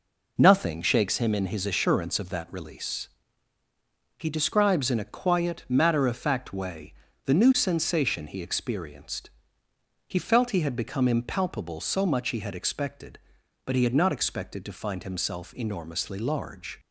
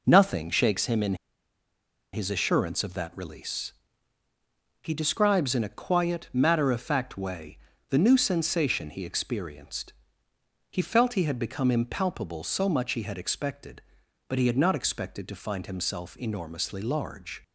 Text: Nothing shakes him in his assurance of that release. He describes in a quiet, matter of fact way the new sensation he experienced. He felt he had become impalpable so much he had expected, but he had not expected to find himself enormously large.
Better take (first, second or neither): first